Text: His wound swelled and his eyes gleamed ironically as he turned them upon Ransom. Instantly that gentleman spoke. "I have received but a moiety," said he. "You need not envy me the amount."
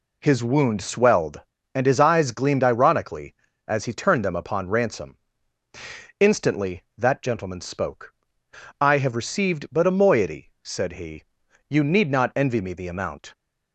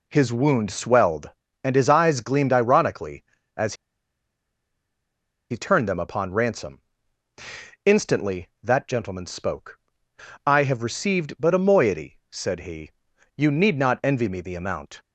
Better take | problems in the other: first | pauses between "as" and "he"; strong; at 3.7 s; 1.7 s long

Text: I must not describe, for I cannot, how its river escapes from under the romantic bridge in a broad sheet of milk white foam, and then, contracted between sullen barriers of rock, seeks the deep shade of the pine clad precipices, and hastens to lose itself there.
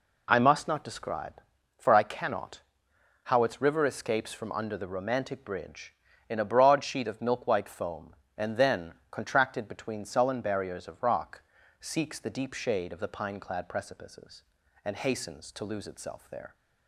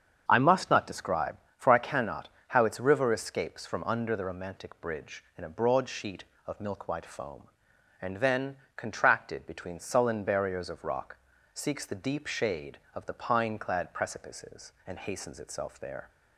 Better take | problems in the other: first | starts louder than the rest; strong; until 1.2 s; 7 dB // skips "to lose"; at 15.3 s

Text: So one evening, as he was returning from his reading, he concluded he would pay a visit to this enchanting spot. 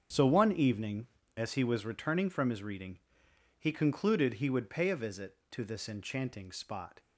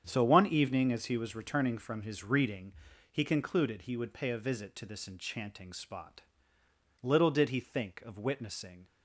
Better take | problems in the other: first | starts louder than the rest; strong; until 1.0 s; 8 dB; also in the first // goes on to say "Little did he think of witnessing"; strong; from 7.0 s on; 1.8 s long

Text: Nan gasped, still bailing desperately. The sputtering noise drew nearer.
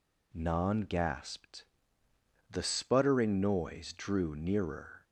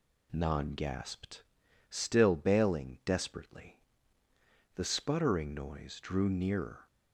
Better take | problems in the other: second | skips "still bailing desperately"; at 2.0 s

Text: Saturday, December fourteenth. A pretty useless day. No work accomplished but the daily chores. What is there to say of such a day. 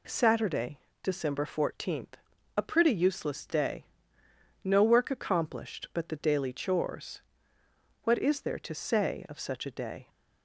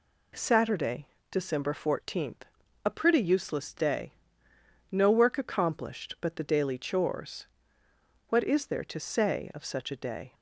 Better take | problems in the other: neither | none

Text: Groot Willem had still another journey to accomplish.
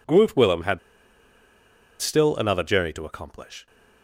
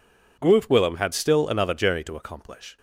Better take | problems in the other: second | pauses between "had" and "still"; at 0.7 s; 1.2 s long

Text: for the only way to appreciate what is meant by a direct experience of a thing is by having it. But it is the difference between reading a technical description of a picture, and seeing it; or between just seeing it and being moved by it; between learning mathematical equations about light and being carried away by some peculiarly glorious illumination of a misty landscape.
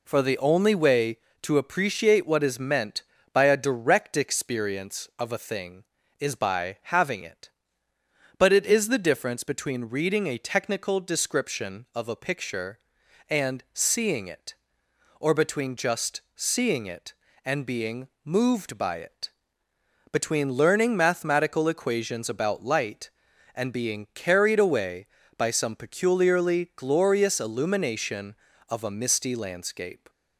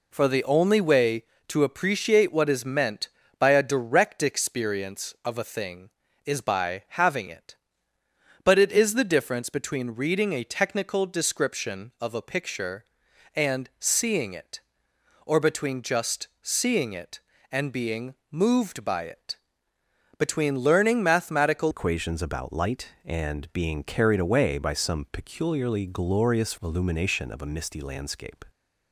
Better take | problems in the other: first | pauses between "being" and "moved"; slight; at 18.1 s; 0.16 s long; slight in the first // changes voice at "equations"; from 21.7 s on; 6.7 s long

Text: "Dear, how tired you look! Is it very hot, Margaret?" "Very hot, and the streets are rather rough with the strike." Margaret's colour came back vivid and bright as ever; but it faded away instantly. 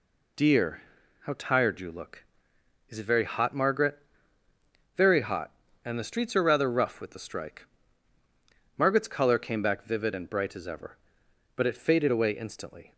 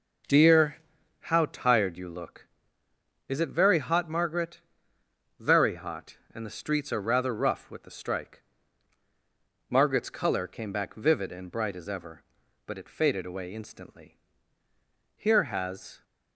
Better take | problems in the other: first | goes on to say "Here has"; noticeable; from 15.1 s on; 0.86 s long

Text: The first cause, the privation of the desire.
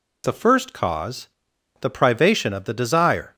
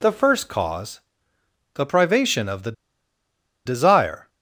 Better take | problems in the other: first | pauses between "the" and "desire"; noticeable; at 2.7 s; 0.93 s long

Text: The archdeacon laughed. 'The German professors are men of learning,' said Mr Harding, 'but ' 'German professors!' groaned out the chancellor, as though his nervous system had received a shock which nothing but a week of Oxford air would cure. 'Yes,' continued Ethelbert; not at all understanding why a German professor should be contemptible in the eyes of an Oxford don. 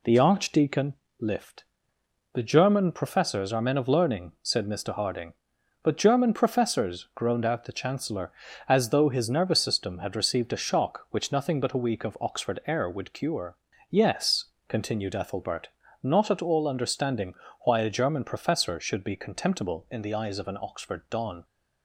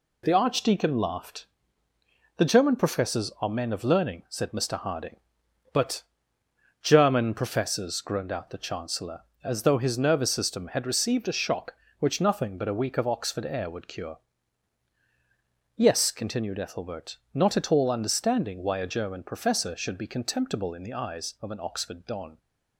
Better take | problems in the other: second | says "lift" for "laughed"; at 1.2 s // pauses between "understanding" and "why"; slight; at 17.3 s; 0.30 s long

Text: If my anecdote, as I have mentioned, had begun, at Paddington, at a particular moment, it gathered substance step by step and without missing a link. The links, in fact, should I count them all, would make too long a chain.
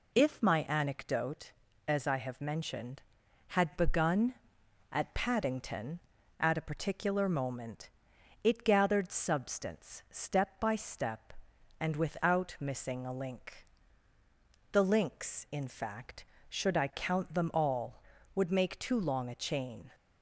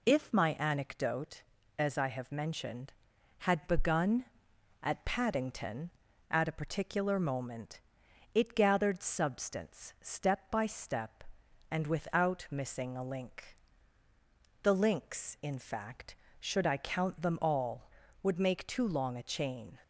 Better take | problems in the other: neither | none

